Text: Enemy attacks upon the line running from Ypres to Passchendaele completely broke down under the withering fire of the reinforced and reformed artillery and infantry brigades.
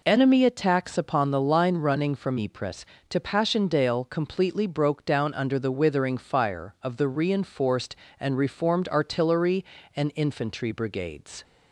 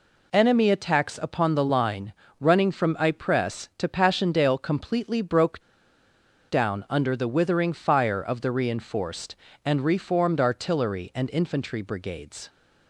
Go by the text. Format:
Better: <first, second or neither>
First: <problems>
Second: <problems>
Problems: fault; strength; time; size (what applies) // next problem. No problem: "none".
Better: first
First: none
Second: pauses between "line" and "running"; slight; at 2.1 s; 0.28 s long // pauses between "broke" and "down"; noticeable; at 5.6 s; 0.88 s long